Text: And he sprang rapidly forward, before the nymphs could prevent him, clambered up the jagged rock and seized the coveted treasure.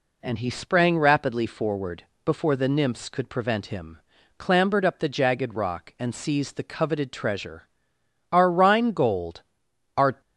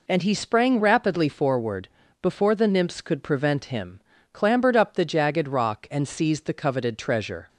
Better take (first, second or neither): second